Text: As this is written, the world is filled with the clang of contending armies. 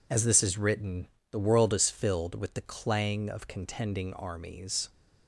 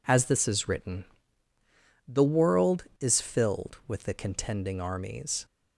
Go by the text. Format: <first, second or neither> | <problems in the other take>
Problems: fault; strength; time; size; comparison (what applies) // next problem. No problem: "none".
first | skips "clang of"; at 4.1 s